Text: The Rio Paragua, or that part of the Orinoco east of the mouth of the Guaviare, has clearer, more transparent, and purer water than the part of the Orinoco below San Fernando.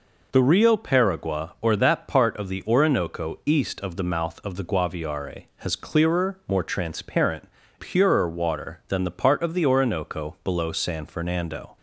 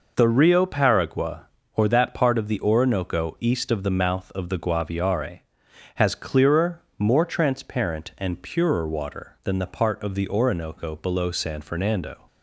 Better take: second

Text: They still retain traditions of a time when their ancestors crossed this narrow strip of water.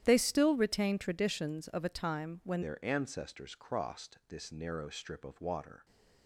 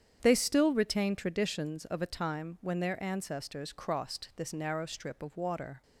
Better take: second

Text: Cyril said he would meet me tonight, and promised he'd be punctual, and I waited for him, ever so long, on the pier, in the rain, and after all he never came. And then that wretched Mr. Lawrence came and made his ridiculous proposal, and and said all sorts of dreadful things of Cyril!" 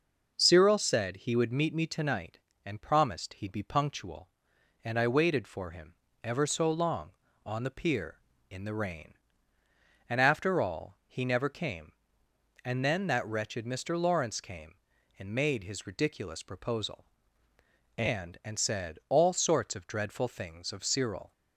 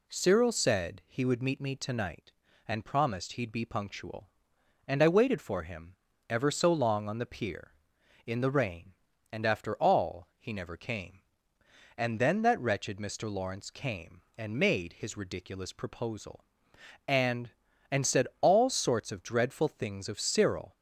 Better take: neither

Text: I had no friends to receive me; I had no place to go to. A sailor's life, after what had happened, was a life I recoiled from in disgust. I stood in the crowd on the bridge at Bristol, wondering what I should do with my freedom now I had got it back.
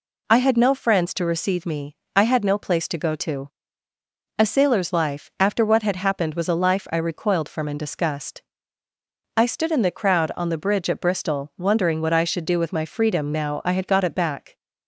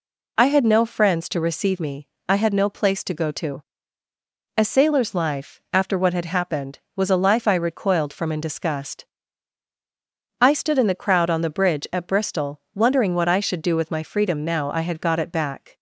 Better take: neither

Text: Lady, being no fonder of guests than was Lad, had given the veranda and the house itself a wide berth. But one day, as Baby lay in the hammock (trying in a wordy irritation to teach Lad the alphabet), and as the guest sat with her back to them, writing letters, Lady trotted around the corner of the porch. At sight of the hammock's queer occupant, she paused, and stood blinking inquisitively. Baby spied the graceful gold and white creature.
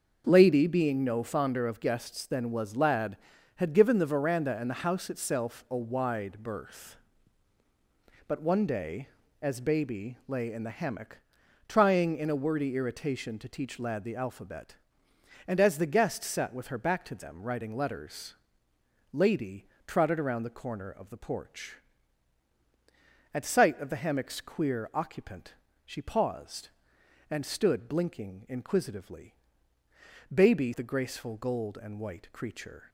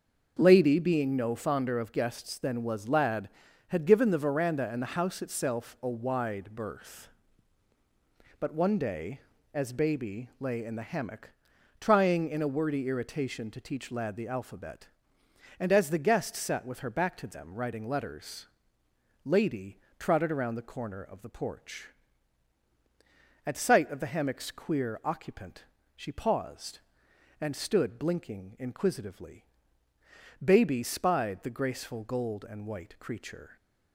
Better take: second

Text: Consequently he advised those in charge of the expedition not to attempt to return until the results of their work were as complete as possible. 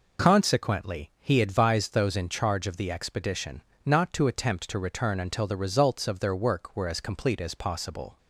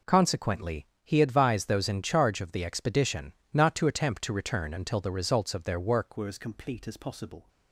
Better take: first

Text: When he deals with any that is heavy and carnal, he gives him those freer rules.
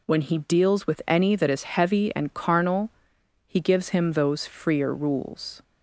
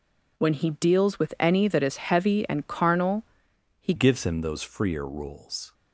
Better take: first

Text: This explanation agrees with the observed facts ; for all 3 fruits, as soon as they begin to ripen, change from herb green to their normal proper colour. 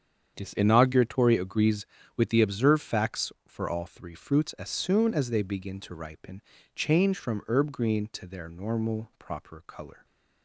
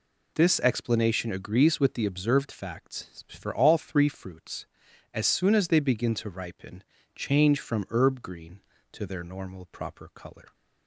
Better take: second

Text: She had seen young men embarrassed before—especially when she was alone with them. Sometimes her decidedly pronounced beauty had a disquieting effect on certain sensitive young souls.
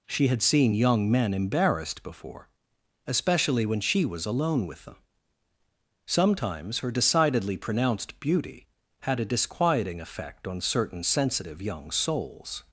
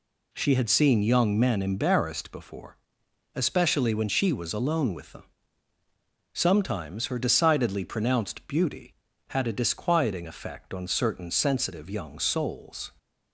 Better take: neither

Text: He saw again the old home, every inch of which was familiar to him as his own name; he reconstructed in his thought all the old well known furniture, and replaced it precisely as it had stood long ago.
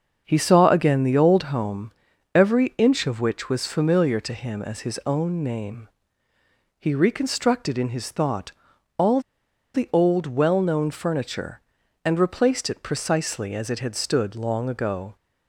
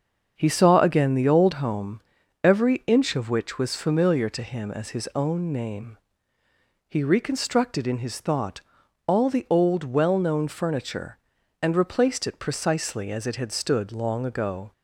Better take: second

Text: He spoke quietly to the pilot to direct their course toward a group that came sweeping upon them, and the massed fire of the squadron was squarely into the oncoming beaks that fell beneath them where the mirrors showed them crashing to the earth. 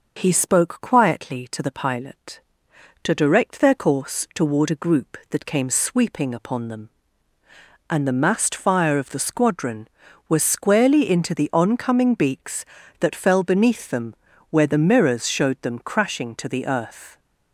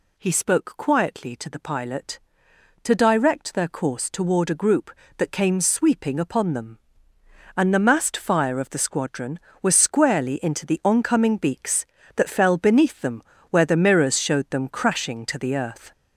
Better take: first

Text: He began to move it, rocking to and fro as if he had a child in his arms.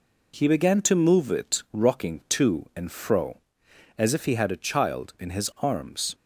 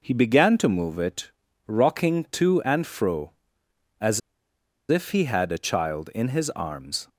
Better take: first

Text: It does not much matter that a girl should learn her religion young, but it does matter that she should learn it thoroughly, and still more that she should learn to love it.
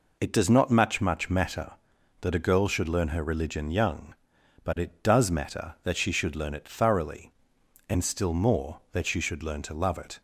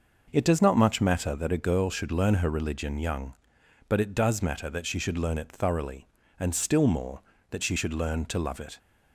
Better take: second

